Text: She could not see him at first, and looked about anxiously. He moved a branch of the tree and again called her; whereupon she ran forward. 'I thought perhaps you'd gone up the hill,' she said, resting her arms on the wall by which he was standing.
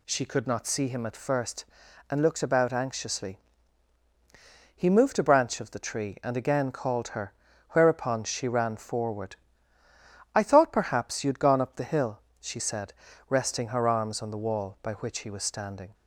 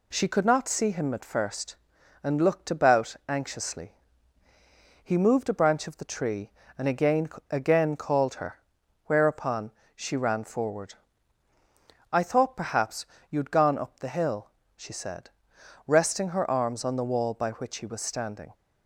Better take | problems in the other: first | says "again" twice; at 7.4 s // pauses between "whereupon" and "she"; slight; at 9.7 s; 0.24 s long // pauses between "perhaps" and "you'd"; slight; at 13.0 s; 0.24 s long

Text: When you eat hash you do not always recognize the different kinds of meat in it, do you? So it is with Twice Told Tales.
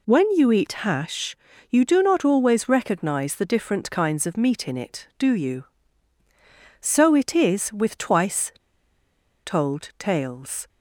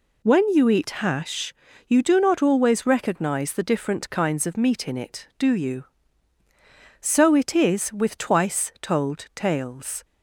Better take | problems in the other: second | pauses between "hash" and "you"; slight; at 1.3 s; 0.32 s long; slight in the second // pauses between "Twice" and "Told"; noticeable; at 8.5 s; 0.93 s long

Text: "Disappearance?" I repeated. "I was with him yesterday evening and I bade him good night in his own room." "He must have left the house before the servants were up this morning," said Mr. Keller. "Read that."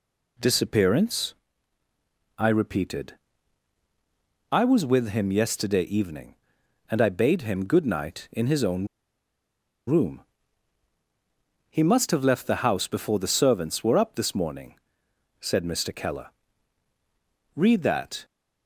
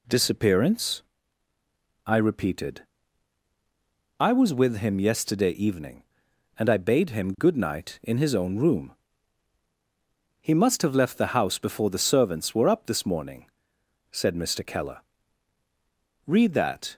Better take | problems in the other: second | pauses between "own" and "room"; at 8.8 s; 1.0 s long

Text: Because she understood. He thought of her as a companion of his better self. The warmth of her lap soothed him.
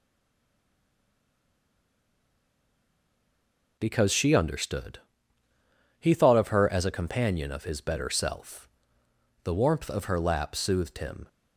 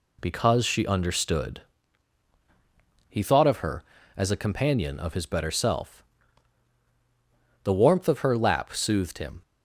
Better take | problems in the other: second | stays silent before the first word; strong; until 3.7 s; 3.7 s long

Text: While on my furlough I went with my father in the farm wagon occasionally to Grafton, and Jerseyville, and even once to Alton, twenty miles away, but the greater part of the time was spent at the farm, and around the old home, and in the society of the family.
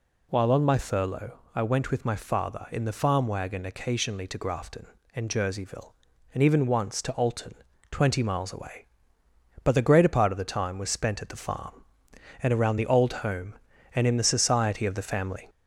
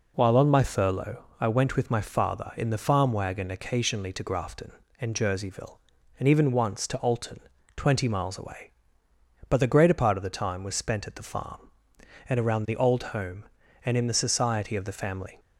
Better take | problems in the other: second | gets louder; slight; throughout; 2 dB // pauses between "furlough" and "I"; slight; at 1.3 s; 0.16 s long; slight in the second

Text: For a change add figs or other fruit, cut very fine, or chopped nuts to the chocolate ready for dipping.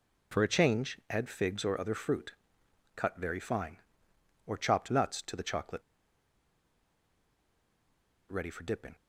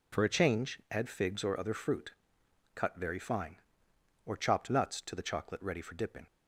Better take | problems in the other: second | pauses between "chocolate" and "ready"; strong; at 5.8 s; 2.4 s long

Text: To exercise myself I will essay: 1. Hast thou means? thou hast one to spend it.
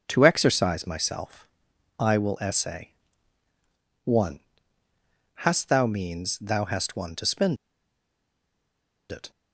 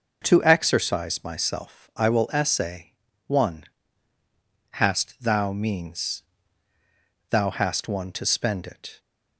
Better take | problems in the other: second | pauses between "myself" and "I"; noticeable; at 1.4 s; 0.52 s long // pauses between "spend" and "it"; strong; at 7.5 s; 1.5 s long

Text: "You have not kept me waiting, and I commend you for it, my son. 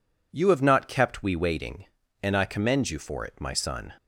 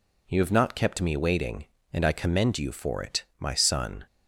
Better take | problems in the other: second | says "we" for "me"; at 1.2 s

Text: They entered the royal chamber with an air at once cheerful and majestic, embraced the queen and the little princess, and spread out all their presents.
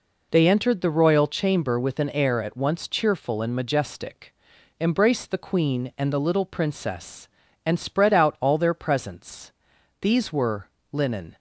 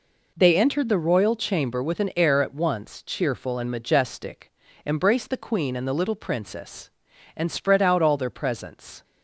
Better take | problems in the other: second | goes on to say "These were linen"; from 10.0 s on; 1.3 s long

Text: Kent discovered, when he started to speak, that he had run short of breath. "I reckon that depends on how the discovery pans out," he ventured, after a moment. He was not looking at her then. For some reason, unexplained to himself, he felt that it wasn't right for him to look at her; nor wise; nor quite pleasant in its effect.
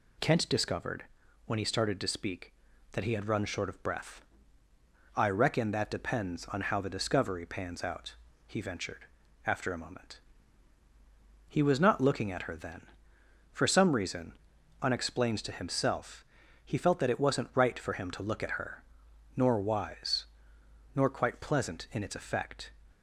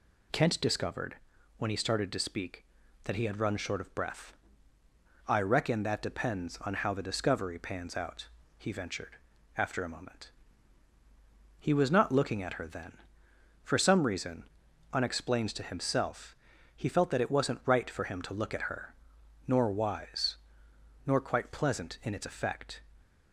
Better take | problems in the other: neither | none

